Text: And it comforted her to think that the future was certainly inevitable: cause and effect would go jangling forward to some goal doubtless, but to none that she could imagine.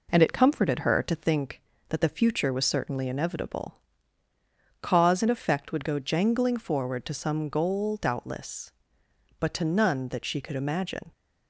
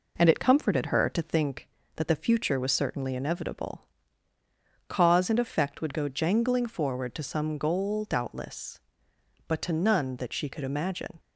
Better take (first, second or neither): neither